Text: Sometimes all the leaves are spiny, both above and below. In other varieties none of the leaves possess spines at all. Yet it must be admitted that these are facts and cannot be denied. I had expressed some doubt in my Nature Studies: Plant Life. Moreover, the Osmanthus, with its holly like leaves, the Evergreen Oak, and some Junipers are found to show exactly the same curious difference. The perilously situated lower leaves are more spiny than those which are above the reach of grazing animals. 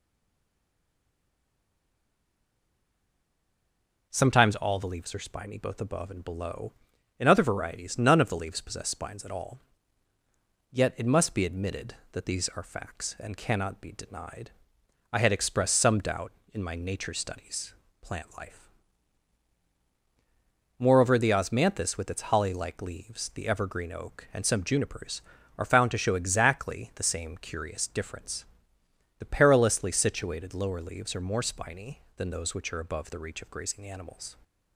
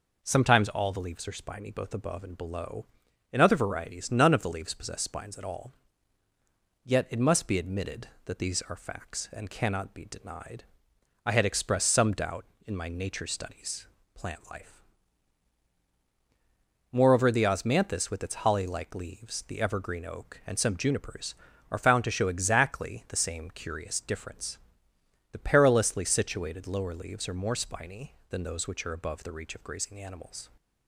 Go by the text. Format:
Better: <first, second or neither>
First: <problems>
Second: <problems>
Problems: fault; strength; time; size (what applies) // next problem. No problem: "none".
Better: second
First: stays silent before the first word; strong; until 4.0 s; 4.0 s long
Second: none